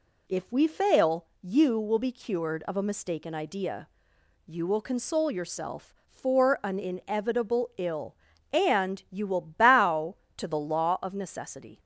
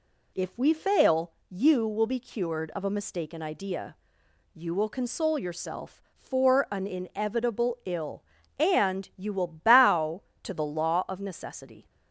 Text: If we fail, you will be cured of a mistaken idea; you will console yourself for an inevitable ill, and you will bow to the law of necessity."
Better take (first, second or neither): neither